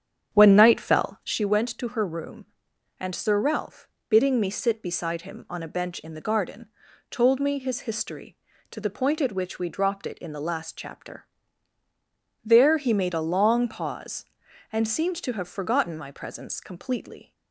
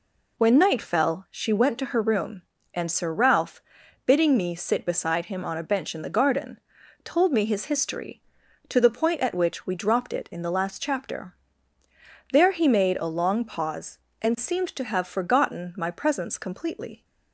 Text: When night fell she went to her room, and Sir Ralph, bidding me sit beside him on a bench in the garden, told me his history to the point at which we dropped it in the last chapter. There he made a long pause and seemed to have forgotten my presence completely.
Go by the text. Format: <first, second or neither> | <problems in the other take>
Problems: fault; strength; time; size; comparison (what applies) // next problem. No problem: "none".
second | starts louder than the rest; strong; until 1.4 s; 8 dB